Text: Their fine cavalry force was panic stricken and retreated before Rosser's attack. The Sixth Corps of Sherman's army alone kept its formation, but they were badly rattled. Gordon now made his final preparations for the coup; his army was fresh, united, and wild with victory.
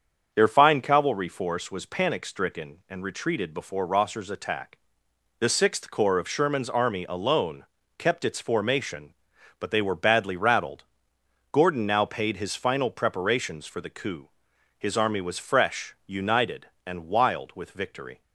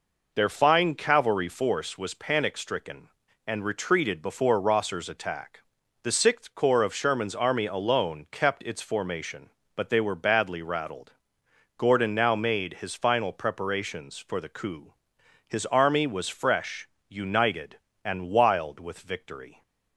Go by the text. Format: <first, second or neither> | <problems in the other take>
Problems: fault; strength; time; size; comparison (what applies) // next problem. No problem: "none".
second | starts louder than the rest; until 1.3 s; 7 dB // pauses between "alone" and "kept"; slight; at 7.6 s; 0.34 s long // says "paid" for "made"; at 12.0 s